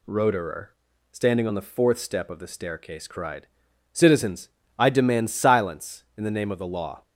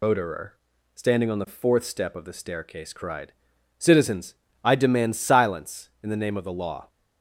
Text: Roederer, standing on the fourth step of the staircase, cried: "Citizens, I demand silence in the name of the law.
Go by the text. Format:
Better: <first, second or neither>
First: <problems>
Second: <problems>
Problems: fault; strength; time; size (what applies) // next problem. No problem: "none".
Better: first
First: none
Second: loses the start of "Roederer"; at 0.0 s; 135 ms